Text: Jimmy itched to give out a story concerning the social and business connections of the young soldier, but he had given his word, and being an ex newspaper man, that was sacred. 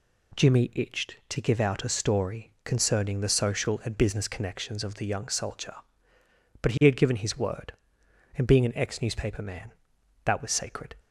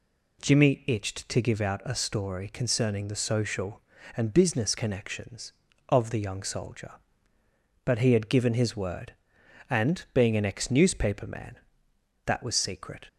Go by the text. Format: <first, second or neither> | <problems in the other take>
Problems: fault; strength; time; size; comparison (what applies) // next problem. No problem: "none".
first | says "secret" for "sacred"; at 12.5 s